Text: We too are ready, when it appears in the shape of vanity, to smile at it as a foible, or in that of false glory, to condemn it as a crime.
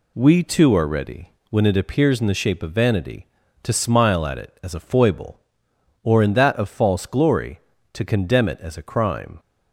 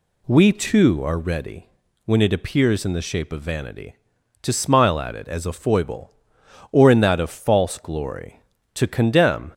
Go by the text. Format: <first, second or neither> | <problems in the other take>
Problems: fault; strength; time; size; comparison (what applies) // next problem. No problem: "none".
first | stops before "it as a crime"; at 9.5 s